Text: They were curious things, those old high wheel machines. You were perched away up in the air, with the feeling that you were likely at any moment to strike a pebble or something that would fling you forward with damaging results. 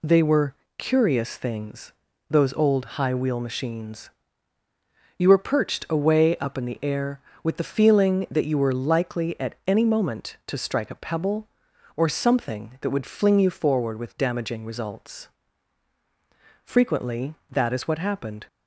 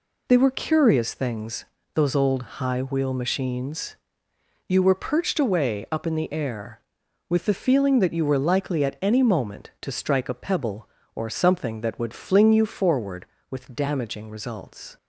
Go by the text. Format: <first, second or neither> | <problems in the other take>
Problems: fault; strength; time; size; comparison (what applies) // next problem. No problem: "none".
second | pauses between "were" and "curious"; slight; at 0.5 s; 0.24 s long // goes on to say "Frequently that is what happened"; strong; from 16.6 s on; 1.8 s long